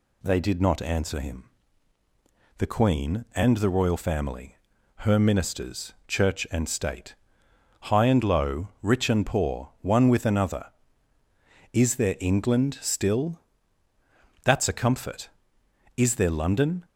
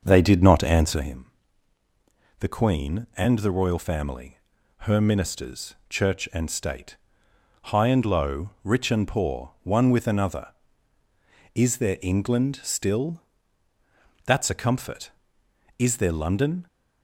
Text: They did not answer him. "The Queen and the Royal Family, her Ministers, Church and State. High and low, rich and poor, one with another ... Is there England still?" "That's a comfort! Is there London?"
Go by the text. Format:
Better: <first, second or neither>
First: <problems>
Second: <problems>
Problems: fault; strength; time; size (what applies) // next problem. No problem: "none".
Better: first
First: none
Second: starts louder than the rest; until 1.1 s; 6.5 dB